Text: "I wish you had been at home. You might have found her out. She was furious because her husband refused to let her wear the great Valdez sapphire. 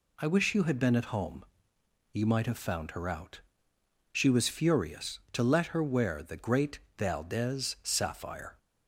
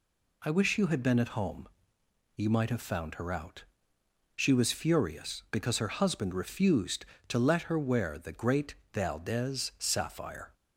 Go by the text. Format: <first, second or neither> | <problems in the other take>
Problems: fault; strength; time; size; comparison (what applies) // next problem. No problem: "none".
second | skips "because her husband refused"; at 5.2 s // pauses between "great" and "Valdez"; slight; at 6.7 s; 0.18 s long; slight in the second